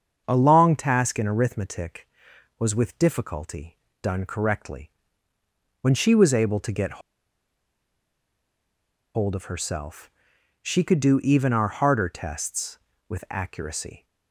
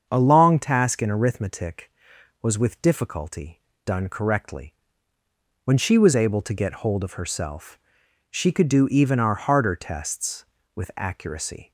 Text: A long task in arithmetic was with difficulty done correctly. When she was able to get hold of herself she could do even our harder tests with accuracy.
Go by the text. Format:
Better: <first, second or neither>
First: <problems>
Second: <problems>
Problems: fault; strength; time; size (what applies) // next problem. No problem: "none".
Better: second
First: starts louder than the rest; until 1.2 s; 7 dB // pauses between "difficulty" and "done"; slight; at 3.7 s; 0.24 s long // pauses between "get" and "hold"; strong; at 7.0 s; 2.1 s long // pauses between "herself" and "she"; noticeable; at 10.0 s; 0.54 s long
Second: starts louder than the rest; until 1.1 s; 7 dB // pauses between "difficulty" and "done"; slight; at 3.5 s; 0.24 s long // pauses between "herself" and "she"; noticeable; at 7.7 s; 0.54 s long